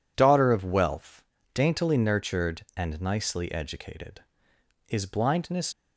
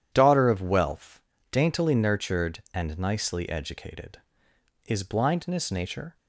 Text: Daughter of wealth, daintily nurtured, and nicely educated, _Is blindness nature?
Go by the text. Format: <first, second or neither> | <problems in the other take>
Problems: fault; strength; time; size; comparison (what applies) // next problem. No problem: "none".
second | stops before "nature"; at 5.7 s